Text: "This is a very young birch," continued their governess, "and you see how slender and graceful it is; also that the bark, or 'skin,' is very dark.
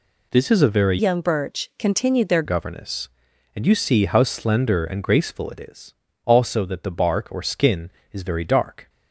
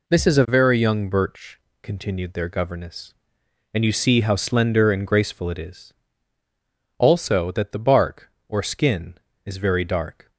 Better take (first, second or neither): second